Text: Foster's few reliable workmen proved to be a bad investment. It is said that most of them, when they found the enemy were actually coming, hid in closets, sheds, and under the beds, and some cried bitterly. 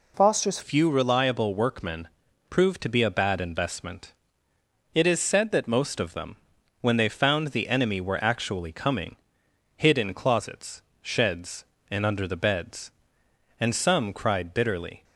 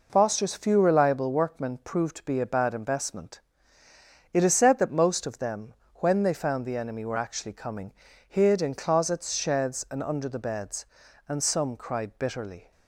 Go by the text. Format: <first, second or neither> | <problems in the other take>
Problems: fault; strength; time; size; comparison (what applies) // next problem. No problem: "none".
second | changes voice at "few"; from 0.6 s on; 14.4 s long // pauses between "workmen" and "proved"; at 2.0 s; 0.42 s long